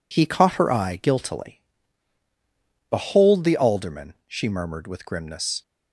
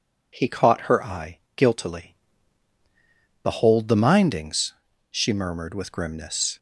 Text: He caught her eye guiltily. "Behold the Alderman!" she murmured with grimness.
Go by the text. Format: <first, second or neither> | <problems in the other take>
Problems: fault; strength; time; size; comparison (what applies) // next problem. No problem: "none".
first | pauses between "eye" and "guiltily"; slight; at 1.3 s; 0.18 s long // says "Mindings" for "Alderman"; at 3.9 s